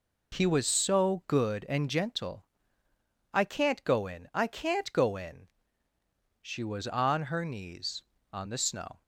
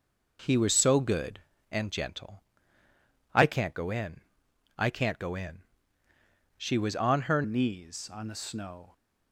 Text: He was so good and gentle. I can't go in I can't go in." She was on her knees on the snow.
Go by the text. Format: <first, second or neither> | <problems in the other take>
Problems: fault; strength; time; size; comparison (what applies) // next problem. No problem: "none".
first | pauses between "in" and "I"; noticeable; at 4.2 s; 0.56 s long // changes voice at "knees"; from 7.4 s on; 1.5 s long